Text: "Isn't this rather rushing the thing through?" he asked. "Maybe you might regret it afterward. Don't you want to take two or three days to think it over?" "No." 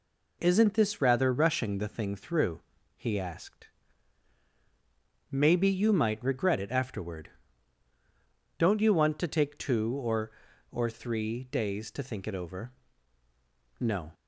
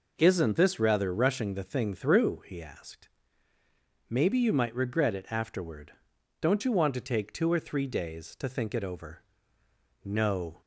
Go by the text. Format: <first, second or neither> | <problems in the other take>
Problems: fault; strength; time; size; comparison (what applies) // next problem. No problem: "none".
second | says "or" twice; at 10.6 s